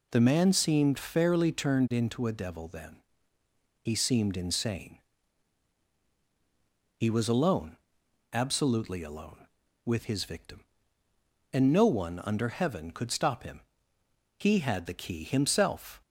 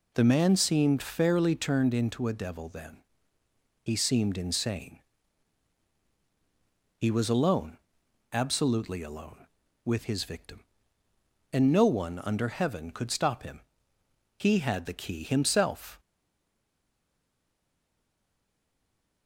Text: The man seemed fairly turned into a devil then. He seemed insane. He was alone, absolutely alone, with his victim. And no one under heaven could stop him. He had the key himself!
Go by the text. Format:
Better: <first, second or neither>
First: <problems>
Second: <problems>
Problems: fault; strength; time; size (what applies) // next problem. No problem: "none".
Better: first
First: none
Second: stays silent after the last word; strong; from 15.9 s on; 3.3 s long